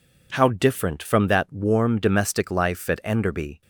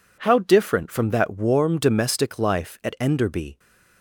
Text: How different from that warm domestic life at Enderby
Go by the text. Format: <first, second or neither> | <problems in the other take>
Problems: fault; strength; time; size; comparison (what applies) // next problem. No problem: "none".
neither | none